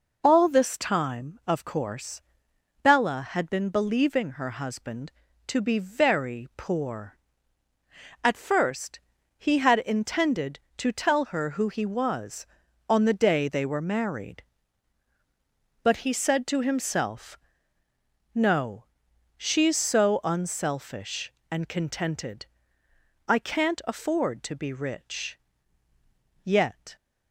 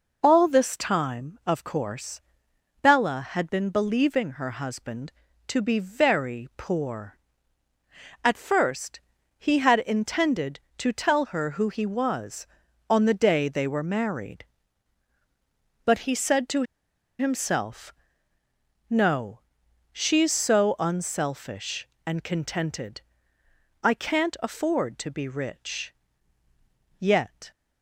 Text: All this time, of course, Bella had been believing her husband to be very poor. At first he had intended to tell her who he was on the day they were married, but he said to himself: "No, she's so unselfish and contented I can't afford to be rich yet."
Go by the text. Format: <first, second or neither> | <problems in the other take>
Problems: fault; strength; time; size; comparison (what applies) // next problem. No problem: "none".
first | pauses between "first" and "he"; at 8.9 s; 0.38 s long; also in the first // pauses between "to" and "himself"; noticeable; at 16.6 s; 0.55 s long // pauses between "contented" and "I"; noticeable; at 23.0 s; 0.82 s long; noticeable in the first // pauses between "rich" and "yet"; at 25.9 s; 1.0 s long; also in the first